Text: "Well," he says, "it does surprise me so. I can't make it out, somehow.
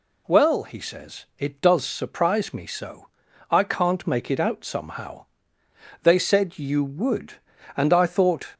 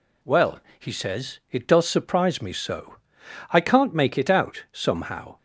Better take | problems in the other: second | goes on to say "They said you would and I thought"; strong; from 6.0 s on; 2.4 s long

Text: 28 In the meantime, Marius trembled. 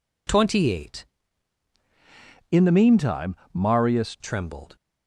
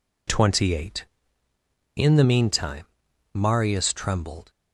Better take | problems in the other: second | changes voice from "In" to "Marius"; from 2.5 to 4.1 s; 1.6 s long

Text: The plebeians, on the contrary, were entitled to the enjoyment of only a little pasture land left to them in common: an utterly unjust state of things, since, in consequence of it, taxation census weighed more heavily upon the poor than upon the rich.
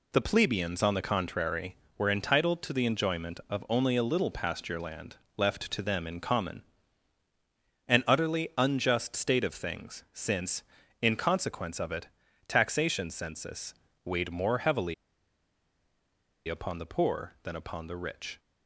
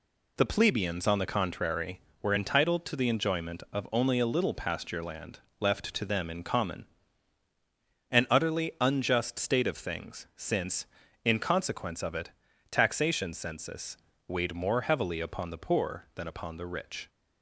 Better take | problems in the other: second | pauses between "land" and "left"; slight; at 5.1 s; 0.18 s long; slight in the second // pauses between "census" and "weighed"; slight; at 13.7 s; 0.32 s long; slight in the second // pauses between "heavily" and "upon"; strong; at 14.9 s; 1.5 s long

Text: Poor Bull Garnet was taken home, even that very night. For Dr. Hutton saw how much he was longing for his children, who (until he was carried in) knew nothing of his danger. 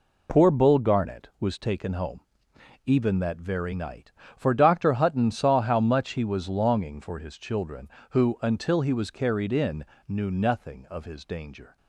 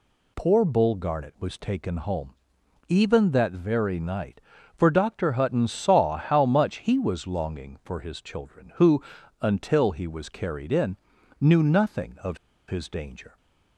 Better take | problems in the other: first | pauses between "of" and "his"; slight; at 12.3 s; 0.30 s long

